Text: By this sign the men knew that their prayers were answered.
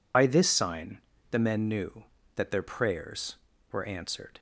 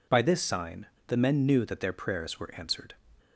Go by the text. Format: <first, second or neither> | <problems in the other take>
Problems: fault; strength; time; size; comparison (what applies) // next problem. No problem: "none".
second | loses the start of "By"; at 0.1 s; 55 ms // pauses between "sign" and "the"; slight; at 0.9 s; 0.32 s long; slight in the second